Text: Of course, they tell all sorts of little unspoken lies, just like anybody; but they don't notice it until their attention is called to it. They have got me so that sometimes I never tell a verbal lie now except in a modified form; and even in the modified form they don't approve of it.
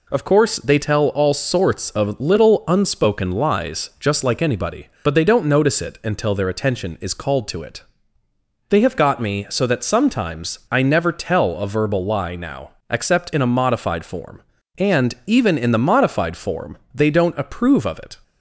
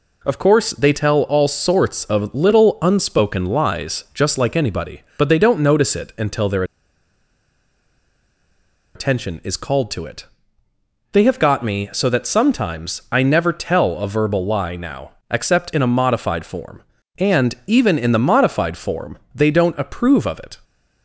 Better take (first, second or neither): first